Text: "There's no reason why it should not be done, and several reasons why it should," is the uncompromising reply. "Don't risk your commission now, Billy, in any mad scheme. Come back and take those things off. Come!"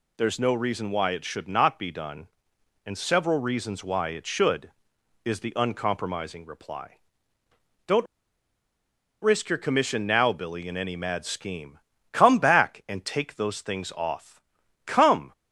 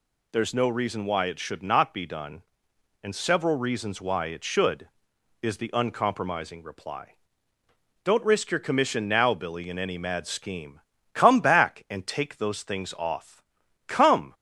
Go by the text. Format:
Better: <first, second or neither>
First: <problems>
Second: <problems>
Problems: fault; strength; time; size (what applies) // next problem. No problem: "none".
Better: second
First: pauses between "Don't" and "risk"; at 8.0 s; 1.1 s long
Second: none